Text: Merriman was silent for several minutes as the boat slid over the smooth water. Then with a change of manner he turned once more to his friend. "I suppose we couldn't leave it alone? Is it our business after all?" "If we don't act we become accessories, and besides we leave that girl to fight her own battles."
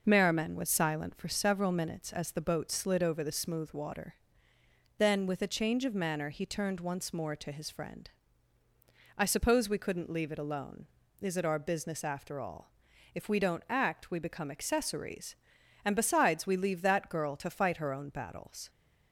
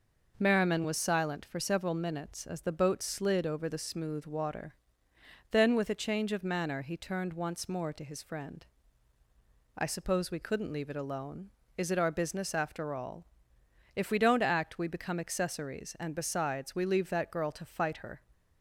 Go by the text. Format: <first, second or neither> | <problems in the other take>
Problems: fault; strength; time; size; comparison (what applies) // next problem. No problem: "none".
first | stops before "own battles"; at 18.3 s